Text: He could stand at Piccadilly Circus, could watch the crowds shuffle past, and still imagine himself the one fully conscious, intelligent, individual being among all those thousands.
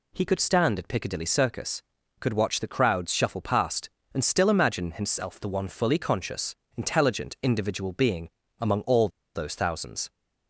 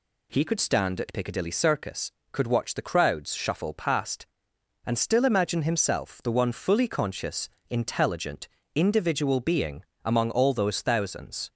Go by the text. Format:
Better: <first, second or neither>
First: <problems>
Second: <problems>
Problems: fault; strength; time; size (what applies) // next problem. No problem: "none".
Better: second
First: pauses between "being" and "among"; slight; at 8.2 s; 0.30 s long // pauses between "all" and "those"; slight; at 9.0 s; 0.27 s long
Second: pauses between "being" and "among"; slight; at 9.8 s; 0.18 s long